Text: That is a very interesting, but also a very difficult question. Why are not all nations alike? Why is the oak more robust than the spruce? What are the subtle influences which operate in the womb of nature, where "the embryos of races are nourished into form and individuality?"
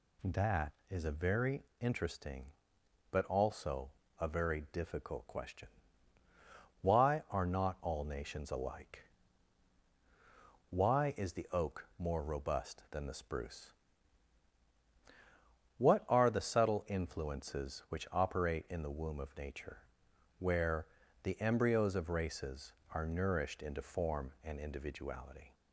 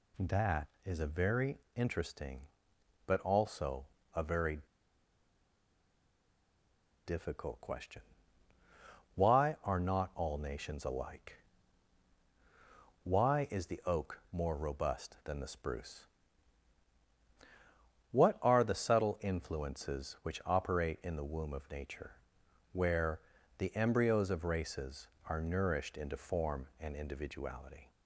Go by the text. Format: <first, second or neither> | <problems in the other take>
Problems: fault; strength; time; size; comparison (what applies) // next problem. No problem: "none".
first | pauses between "very" and "interesting"; slight; at 1.5 s; 0.18 s long; slight in the first // pauses between "also" and "a"; slight; at 3.8 s; 0.32 s long; slight in the first // pauses between "very" and "difficult"; strong; at 4.5 s; 2.4 s long // pauses between "where" and "the"; at 23.1 s; 0.40 s long; also in the first